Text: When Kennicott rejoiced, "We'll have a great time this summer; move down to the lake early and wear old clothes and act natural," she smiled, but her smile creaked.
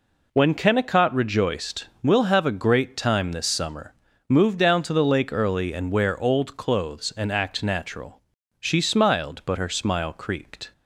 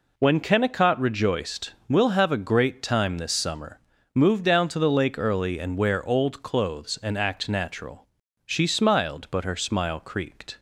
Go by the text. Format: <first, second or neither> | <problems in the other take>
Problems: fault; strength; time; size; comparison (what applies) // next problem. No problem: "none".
neither | none